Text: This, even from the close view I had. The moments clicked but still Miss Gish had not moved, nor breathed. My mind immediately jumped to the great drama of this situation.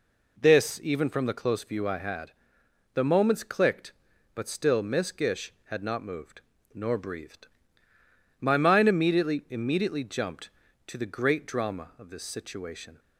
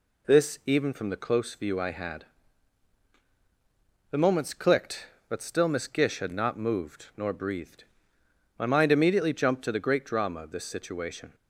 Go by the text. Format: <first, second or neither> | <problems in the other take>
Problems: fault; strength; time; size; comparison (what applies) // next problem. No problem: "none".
second | says "immediately" twice; at 9.5 s